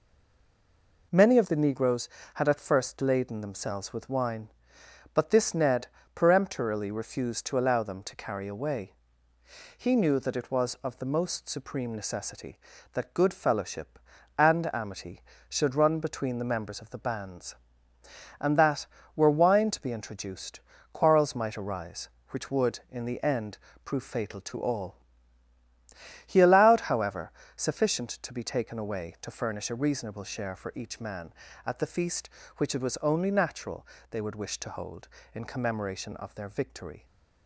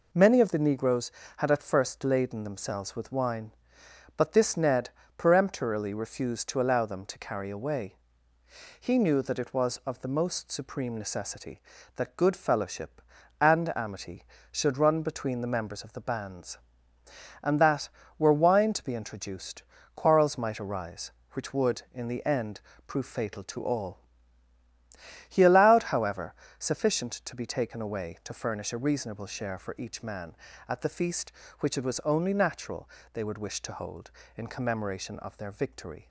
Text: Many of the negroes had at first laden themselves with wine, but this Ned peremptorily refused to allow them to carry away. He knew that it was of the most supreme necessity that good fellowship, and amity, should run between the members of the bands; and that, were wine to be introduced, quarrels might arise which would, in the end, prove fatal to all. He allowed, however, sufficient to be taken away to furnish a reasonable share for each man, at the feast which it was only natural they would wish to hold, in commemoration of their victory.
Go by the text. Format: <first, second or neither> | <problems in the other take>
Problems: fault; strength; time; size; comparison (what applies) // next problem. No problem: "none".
second | stays silent before the first word; until 1.1 s; 1.1 s long // pauses between "Ned" and "peremptorily"; slight; at 5.8 s; 0.28 s long; slight in the second // pauses between "natural" and "they"; slight; at 33.8 s; 0.24 s long; slight in the second